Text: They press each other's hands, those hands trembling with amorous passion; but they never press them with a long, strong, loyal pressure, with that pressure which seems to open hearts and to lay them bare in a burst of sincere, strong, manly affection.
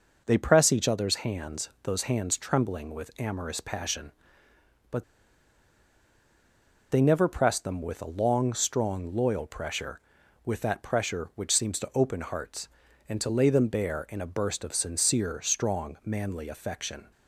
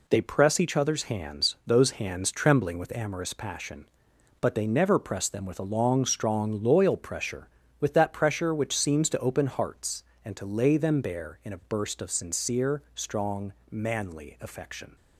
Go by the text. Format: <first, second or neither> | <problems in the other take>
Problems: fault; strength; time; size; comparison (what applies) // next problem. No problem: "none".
second | pauses between "but" and "they"; strong; at 5.0 s; 1.8 s long